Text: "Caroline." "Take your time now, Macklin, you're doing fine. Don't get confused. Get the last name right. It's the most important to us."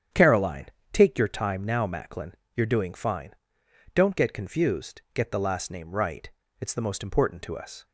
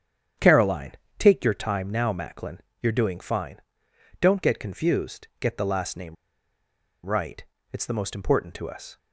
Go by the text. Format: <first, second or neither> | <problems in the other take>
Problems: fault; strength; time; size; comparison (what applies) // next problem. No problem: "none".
first | starts louder than the rest; strong; until 1.6 s; 8.5 dB; strong in the first // pauses between "name" and "right"; noticeable; at 6.1 s; 0.90 s long